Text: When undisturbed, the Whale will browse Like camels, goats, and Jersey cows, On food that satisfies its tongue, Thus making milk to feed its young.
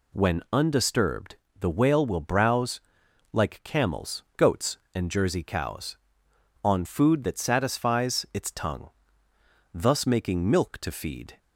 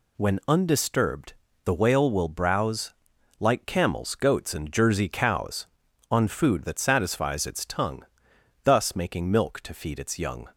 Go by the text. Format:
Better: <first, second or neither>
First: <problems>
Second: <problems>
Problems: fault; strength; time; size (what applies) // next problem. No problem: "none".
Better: second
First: pauses between "browse" and "Like"; noticeable; at 2.7 s; 0.52 s long // stops before "its young"; at 11.3 s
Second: pauses between "browse" and "Like"; noticeable; at 2.9 s; 0.46 s long